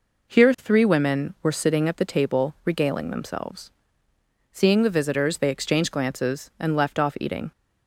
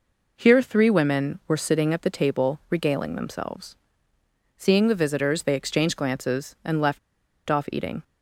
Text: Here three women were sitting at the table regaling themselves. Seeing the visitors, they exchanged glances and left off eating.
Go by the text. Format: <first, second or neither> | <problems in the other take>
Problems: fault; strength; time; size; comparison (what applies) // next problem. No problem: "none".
first | pauses between "left" and "off"; noticeable; at 6.9 s; 0.49 s long